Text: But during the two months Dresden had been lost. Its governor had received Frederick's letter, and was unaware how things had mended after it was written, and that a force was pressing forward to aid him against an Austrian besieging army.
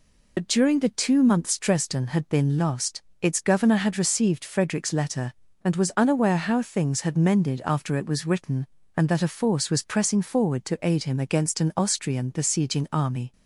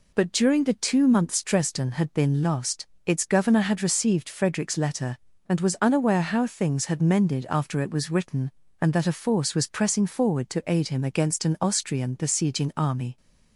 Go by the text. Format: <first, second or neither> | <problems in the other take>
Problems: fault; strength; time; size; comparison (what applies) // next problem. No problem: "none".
second | loses the start of "But"; at 0.3 s; 70 ms